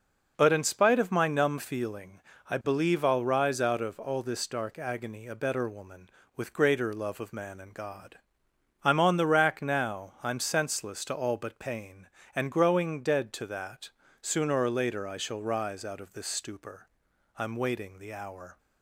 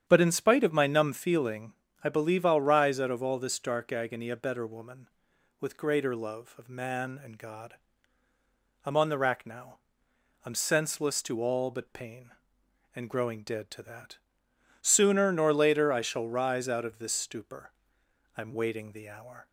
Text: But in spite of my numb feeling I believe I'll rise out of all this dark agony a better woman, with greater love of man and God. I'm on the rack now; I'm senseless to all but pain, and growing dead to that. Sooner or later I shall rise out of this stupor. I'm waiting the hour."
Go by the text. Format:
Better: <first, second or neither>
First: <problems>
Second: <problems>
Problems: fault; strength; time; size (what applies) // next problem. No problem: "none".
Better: first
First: pauses between "feeling" and "I"; slight; at 2.2 s; 0.28 s long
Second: starts louder than the rest; strong; until 1.0 s; 9.5 dB // pauses between "feeling" and "I"; slight; at 1.7 s; 0.30 s long // says "nor" for "or"; at 15.3 s